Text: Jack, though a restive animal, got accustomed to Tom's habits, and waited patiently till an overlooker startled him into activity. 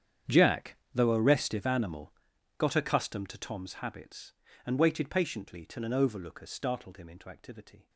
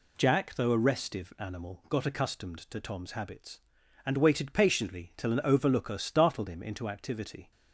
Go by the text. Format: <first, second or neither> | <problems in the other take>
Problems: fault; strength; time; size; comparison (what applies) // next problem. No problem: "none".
second | gets quieter; strong; throughout; 18 dB